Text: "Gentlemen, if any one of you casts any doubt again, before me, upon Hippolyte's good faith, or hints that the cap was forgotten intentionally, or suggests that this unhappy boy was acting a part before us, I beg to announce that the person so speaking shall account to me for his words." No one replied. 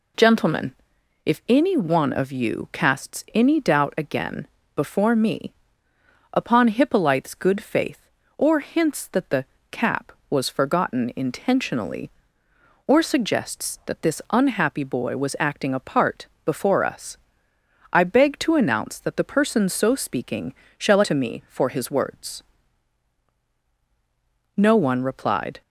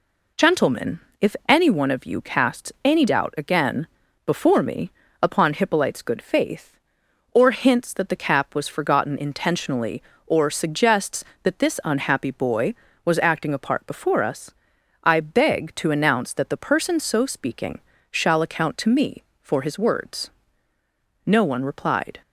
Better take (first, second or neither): second